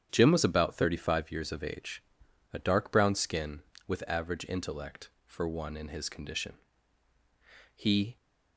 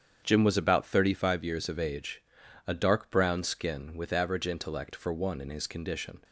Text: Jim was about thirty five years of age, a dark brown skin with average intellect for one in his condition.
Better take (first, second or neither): second